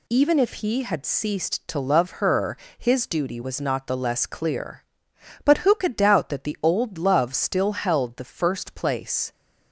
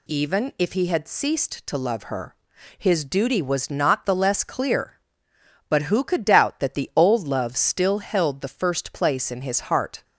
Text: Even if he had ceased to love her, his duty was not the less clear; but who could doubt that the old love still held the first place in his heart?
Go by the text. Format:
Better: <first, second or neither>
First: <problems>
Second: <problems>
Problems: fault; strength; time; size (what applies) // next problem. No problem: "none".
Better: second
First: stops before "in his heart"; at 9.3 s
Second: none